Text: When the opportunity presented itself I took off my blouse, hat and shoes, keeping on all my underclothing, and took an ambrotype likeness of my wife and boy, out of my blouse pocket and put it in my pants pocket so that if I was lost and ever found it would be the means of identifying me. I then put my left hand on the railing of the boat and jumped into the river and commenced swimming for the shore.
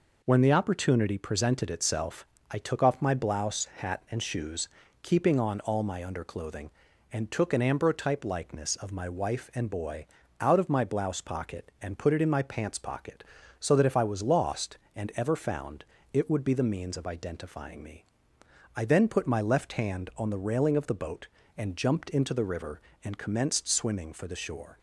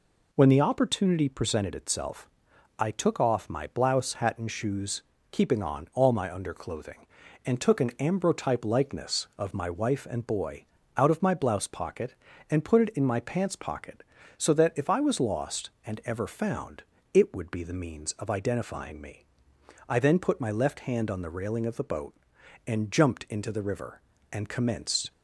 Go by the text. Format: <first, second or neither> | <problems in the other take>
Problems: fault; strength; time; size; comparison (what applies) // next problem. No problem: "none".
first | pauses between "itself" and "I"; noticeable; at 2.2 s; 0.50 s long; slight in the first // pauses between "found" and "it"; slight; at 16.8 s; 0.28 s long; slight in the first // stops before "swimming for the shore"; at 25.1 s